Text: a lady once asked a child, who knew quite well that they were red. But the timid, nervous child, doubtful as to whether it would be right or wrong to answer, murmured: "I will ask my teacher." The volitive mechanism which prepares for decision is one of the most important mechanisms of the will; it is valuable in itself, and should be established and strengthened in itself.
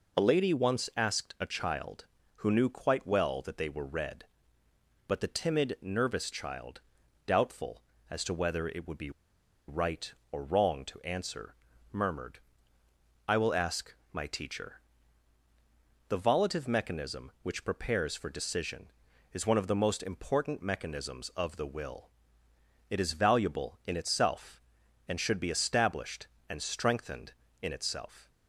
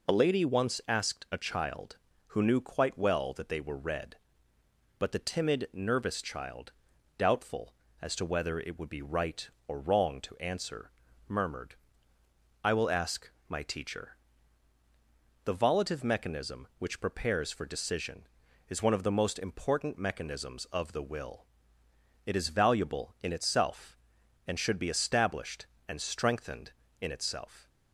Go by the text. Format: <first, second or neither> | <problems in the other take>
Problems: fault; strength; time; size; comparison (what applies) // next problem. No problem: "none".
second | pauses between "be" and "right"; noticeable; at 9.0 s; 0.58 s long // pauses between "ask" and "my"; slight; at 13.9 s; 0.16 s long; slight in the second